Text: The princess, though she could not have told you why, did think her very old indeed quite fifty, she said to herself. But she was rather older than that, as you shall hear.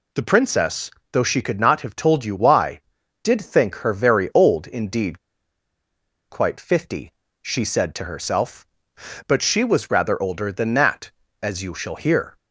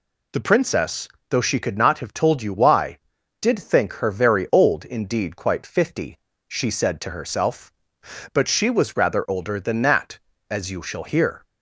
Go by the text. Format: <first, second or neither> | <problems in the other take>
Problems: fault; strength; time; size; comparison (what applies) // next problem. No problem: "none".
second | pauses between "indeed" and "quite"; at 5.1 s; 1.1 s long